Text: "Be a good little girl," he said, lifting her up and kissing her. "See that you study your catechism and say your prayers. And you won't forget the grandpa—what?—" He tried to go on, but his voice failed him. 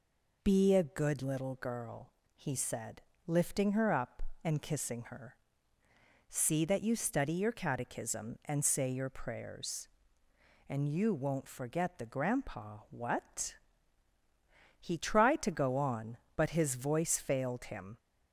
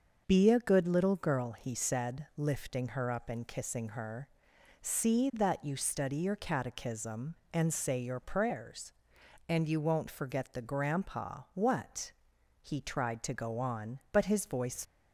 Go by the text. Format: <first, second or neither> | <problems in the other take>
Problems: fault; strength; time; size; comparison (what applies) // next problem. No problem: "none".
first | starts louder than the rest; until 1.2 s; 6.5 dB // stops before "failed him"; at 14.8 s